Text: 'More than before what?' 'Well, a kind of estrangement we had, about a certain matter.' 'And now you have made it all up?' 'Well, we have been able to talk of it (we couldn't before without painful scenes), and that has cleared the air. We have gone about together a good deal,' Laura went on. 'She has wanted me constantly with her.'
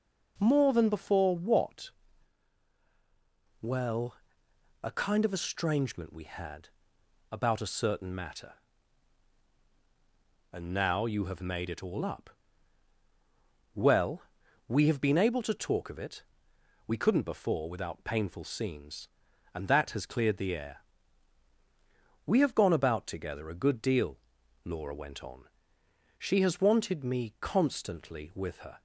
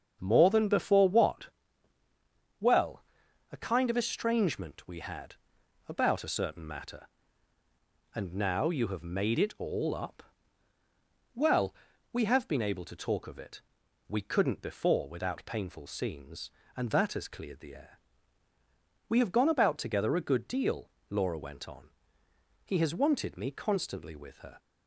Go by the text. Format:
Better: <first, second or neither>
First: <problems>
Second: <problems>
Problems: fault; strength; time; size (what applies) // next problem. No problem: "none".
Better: first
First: none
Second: starts louder than the rest; until 1.2 s; 7 dB // says "He" for "She"; at 22.6 s